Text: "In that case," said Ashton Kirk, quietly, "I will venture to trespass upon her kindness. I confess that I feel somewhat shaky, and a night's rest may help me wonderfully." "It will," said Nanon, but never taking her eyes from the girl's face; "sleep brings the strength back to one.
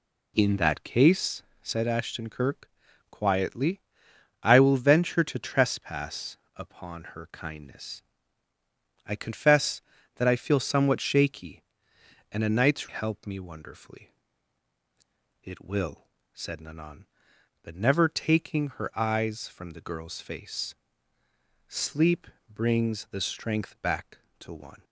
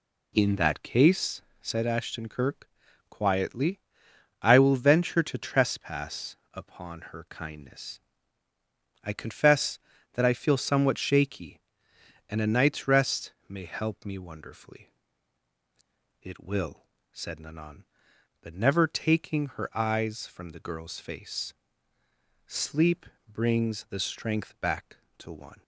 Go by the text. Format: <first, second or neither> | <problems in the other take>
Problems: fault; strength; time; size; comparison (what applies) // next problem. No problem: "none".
second | pauses between "trespass" and "upon"; slight; at 6.3 s; 0.22 s long; slight in the second // skips "rest may"; at 12.8 s // pauses between "sleep" and "brings"; slight; at 22.2 s; 0.24 s long; slight in the second